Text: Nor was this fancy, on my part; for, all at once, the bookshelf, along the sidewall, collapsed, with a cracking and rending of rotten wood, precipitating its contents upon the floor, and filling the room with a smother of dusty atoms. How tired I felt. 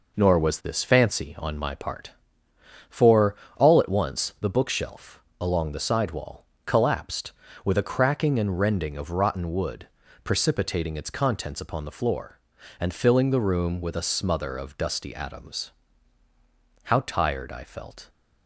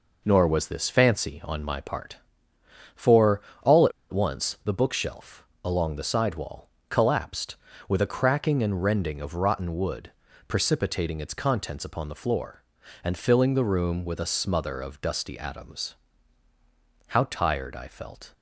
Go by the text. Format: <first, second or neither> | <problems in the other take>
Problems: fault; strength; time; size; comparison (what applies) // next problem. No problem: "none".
first | pauses between "at" and "once"; slight; at 3.9 s; 0.20 s long